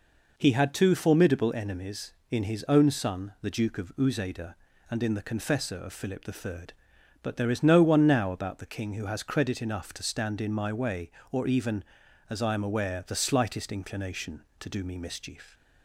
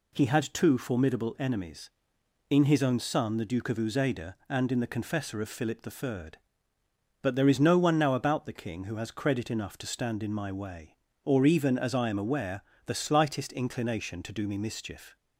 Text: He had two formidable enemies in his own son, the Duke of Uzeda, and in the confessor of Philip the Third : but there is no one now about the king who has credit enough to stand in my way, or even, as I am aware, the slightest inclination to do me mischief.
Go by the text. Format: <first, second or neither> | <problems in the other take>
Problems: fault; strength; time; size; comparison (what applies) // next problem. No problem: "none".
neither | none